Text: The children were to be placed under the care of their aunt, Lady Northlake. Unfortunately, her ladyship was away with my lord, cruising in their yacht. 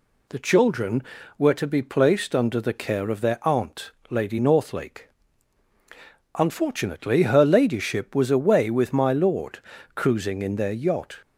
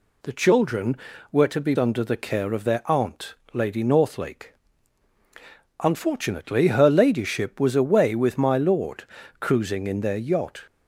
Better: first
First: none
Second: skips "placed"; at 1.7 s

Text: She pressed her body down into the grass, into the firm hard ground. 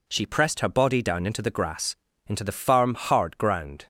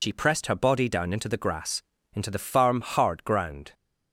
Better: first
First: none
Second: loses the start of "She"; at 0.0 s; 65 ms

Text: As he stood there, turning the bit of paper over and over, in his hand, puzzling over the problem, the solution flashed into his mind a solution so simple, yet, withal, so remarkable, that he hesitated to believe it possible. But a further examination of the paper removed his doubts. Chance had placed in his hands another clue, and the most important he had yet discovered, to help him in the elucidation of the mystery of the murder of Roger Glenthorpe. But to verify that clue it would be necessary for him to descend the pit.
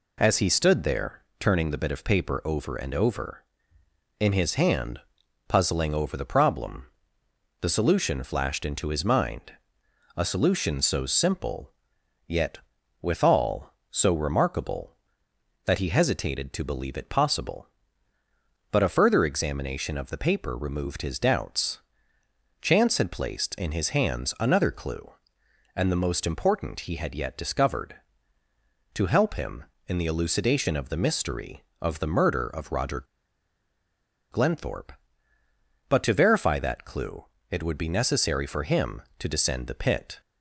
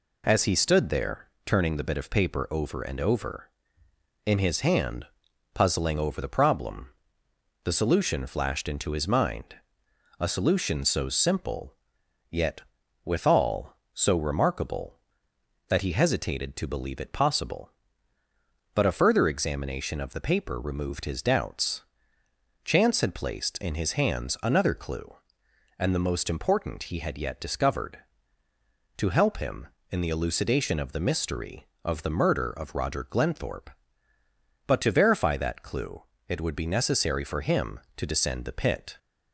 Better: second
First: pauses between "mind" and "a"; noticeable; at 9.5 s; 0.64 s long // pauses between "Roger" and "Glenthorpe"; strong; at 33.0 s; 1.2 s long // pauses between "clue" and "it"; slight; at 37.2 s; 0.26 s long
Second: pauses between "mind" and "a"; noticeable; at 9.5 s; 0.64 s long // pauses between "clue" and "it"; slight; at 36.0 s; 0.26 s long

